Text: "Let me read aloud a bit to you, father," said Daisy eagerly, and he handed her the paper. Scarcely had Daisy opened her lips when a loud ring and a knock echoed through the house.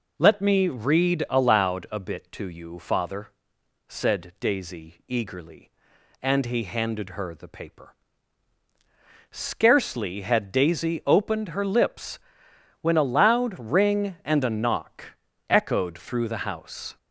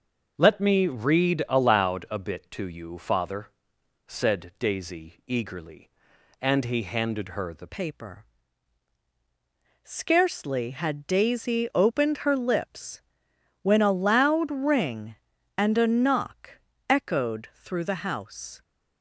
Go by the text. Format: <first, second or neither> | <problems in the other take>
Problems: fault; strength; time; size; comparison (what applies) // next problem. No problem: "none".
first | changes voice at "paper"; from 7.6 s on; 11.0 s long // pauses between "lips" and "when"; noticeable; at 13.0 s; 0.58 s long; noticeable in the first // pauses between "knock" and "echoed"; slight; at 16.5 s; 0.30 s long; slight in the first